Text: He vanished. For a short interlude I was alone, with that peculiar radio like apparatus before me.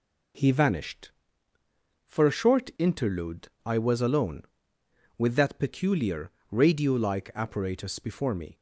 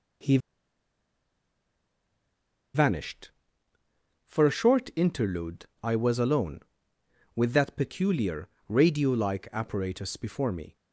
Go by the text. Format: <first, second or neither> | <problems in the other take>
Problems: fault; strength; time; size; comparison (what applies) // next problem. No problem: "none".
first | pauses between "He" and "vanished"; strong; at 0.3 s; 2.3 s long // pauses between "interlude" and "I"; slight; at 5.6 s; 0.18 s long; slight in the first // pauses between "peculiar" and "radio"; slight; at 8.4 s; 0.22 s long; slight in the first